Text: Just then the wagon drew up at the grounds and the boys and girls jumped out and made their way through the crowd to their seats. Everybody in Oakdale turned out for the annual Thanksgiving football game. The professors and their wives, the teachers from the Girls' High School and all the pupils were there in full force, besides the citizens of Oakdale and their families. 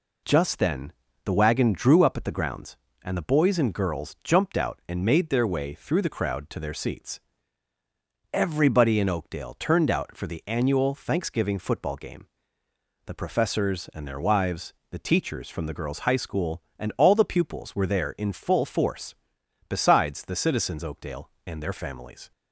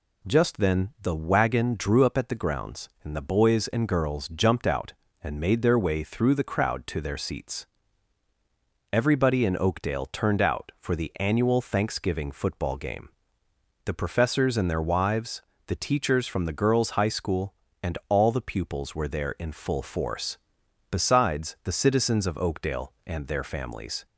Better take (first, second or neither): second